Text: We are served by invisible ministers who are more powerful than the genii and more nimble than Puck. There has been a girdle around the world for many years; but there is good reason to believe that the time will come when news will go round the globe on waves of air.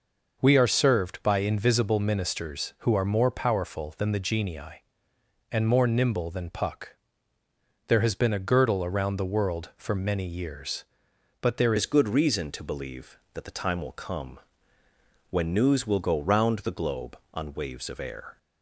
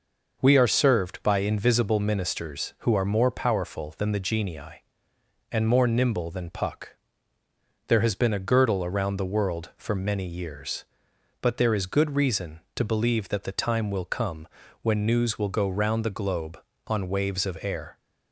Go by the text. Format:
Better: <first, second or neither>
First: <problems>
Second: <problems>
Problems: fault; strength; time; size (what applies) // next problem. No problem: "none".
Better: second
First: changes voice at "is"; from 11.7 s on; 6.6 s long // pauses between "come" and "when"; noticeable; at 14.3 s; 0.94 s long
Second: pauses between "come" and "when"; at 14.4 s; 0.38 s long